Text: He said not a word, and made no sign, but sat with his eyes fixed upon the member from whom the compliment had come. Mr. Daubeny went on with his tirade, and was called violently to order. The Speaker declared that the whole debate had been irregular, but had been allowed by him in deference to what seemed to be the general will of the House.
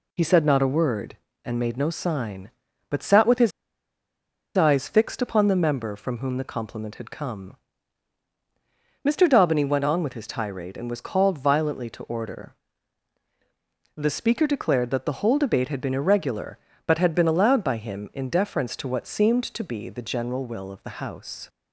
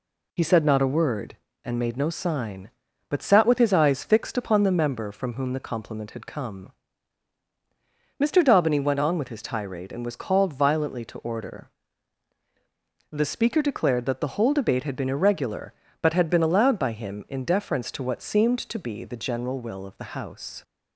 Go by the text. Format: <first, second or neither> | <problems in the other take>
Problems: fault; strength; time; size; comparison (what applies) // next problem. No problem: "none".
second | pauses between "his" and "eyes"; at 3.5 s; 1.0 s long